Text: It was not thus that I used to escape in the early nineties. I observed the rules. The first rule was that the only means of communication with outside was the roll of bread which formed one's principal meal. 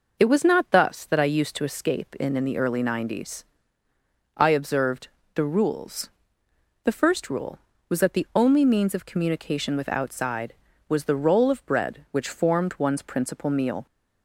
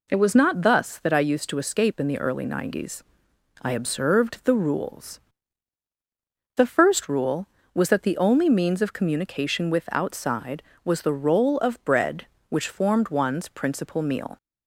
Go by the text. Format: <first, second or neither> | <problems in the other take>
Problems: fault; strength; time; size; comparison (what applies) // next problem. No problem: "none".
second | says "in" twice; at 2.3 s // pauses between "observed" and "the"; slight; at 5.0 s; 0.26 s long